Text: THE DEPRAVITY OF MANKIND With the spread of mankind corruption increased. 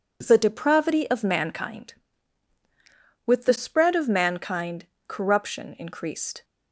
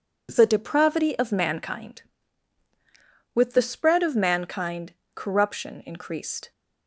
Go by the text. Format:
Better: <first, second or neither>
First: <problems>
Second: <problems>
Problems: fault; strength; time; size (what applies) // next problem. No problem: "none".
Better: neither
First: pauses between "mankind" and "corruption"; slight; at 4.8 s; 0.22 s long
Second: pauses between "mankind" and "corruption"; slight; at 4.9 s; 0.22 s long